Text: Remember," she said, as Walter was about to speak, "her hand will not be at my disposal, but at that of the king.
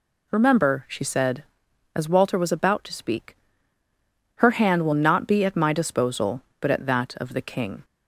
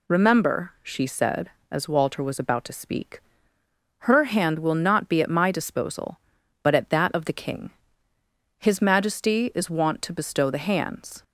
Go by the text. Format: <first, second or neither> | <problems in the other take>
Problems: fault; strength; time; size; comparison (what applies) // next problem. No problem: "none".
first | goes on to say "His majesty is wont to bestow the hands"; strong; from 8.5 s on; 2.6 s long